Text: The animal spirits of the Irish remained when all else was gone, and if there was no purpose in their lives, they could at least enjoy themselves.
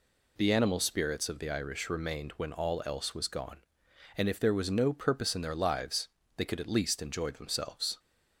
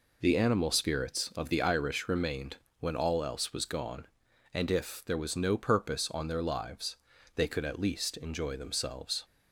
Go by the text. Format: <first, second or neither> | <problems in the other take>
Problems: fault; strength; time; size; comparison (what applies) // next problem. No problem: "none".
first | pauses between "remained" and "when"; slight; at 2.5 s; 0.22 s long // says "on" for "in"; at 6.1 s